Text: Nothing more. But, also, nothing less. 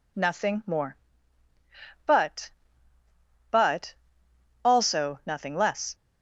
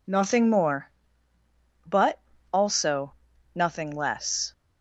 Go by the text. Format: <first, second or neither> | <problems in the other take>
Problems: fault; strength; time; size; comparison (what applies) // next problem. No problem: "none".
second | says "But" twice; at 3.5 s